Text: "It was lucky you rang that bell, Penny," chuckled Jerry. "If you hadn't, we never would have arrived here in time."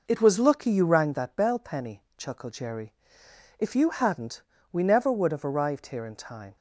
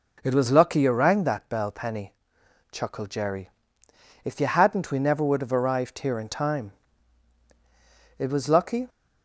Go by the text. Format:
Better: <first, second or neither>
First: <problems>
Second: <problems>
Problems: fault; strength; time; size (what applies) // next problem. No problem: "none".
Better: first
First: none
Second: goes on to say "It was lucky"; noticeable; from 8.1 s on; 0.70 s long